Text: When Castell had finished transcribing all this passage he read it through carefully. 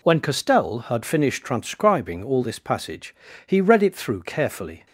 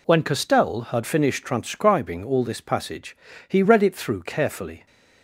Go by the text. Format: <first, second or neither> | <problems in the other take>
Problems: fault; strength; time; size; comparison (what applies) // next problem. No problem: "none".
neither | pauses between "passage" and "he"; slight; the same in both